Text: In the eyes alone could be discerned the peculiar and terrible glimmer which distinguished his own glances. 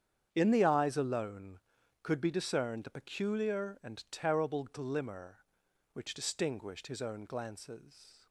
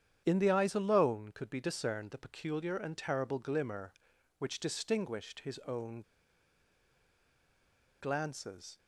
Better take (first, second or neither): first